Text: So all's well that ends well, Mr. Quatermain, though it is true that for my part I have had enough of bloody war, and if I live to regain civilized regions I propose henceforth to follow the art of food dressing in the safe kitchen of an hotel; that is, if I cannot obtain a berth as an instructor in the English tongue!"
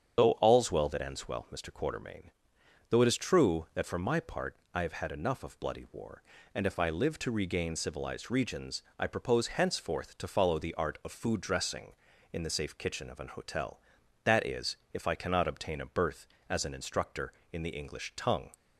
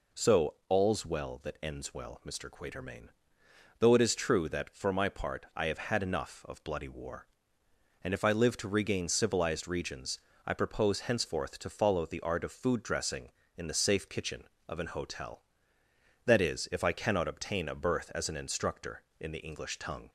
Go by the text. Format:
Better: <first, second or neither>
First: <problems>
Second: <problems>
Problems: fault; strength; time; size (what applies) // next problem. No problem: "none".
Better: second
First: loses the start of "So"; at 0.1 s; 120 ms // starts louder than the rest; strong; until 1.1 s; 8 dB // pauses between "part" and "I"; slight; at 4.5 s; 0.20 s long // pauses between "regions" and "I"; slight; at 8.8 s; 0.16 s long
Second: pauses between "regions" and "I"; slight; at 10.1 s; 0.26 s long